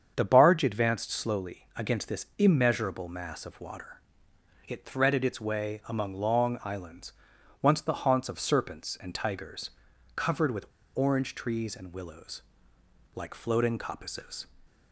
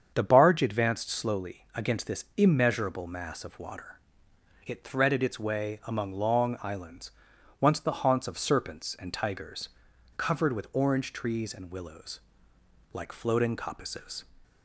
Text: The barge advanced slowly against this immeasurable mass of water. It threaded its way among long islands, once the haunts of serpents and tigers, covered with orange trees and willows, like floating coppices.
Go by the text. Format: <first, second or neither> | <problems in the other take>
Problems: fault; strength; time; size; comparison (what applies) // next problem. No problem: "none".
second | starts louder than the rest; strong; until 1.1 s; 7.5 dB; strong in the second // pauses between "with" and "orange"; slight; at 10.6 s; 0.28 s long